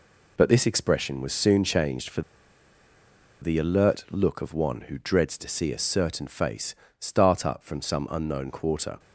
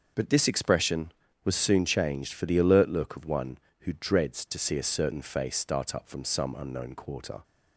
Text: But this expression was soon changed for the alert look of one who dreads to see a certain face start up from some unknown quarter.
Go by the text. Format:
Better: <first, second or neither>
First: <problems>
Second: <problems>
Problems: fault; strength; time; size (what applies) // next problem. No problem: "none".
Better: second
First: pauses between "for" and "the"; at 2.2 s; 1.2 s long // pauses between "face" and "start"; slight; at 6.7 s; 0.24 s long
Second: none